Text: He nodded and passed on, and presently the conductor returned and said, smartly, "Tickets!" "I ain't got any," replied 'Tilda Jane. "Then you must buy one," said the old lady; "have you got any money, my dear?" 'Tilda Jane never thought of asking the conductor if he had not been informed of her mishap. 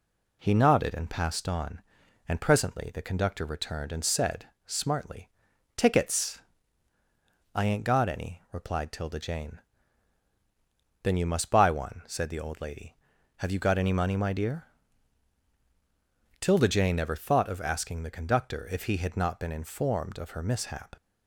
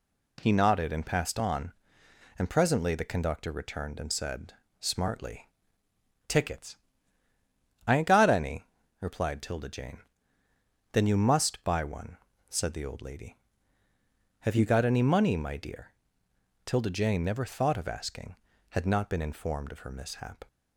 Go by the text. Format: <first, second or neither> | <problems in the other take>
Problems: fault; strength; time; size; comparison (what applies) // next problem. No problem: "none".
first | skips "the conductor if he"; at 18.5 s